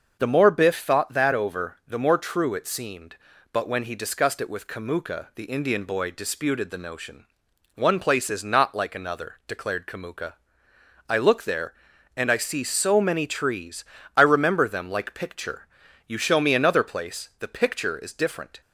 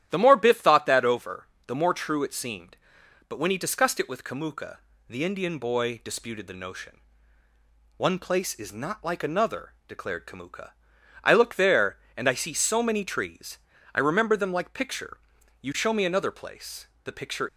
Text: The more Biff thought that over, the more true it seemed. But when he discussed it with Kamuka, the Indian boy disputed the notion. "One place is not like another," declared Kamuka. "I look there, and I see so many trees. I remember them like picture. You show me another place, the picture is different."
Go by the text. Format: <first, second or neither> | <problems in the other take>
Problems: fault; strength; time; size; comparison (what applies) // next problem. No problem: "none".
first | starts louder than the rest; strong; until 1.1 s; 11.5 dB; also in the first // stops before "is different"; at 17.4 s